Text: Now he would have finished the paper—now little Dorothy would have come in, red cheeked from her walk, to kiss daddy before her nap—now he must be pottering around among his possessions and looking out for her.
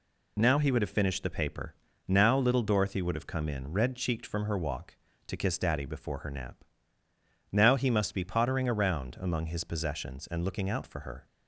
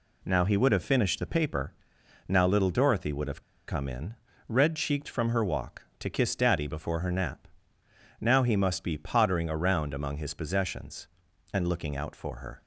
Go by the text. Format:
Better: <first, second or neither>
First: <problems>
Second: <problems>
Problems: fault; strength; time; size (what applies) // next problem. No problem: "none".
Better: first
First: none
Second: pauses between "have" and "come"; slight; at 3.4 s; 0.27 s long